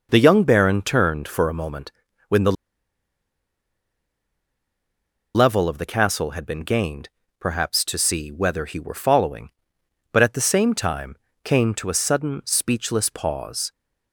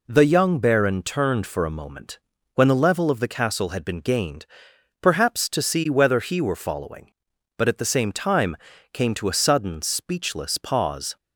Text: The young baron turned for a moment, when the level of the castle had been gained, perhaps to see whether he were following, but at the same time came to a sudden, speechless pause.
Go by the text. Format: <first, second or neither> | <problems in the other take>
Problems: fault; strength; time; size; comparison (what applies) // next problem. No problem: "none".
second | pauses between "the" and "level"; strong; at 2.5 s; 2.8 s long // pauses between "time" and "came"; slight; at 11.1 s; 0.30 s long; also in the second